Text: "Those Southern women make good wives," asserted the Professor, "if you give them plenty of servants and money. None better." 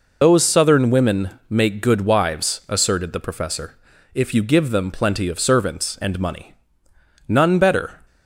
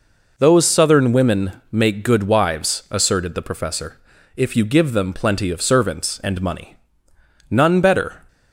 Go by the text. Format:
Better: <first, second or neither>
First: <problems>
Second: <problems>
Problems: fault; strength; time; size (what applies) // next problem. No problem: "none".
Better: second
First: loses the start of "Those"; at 0.2 s; 50 ms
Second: none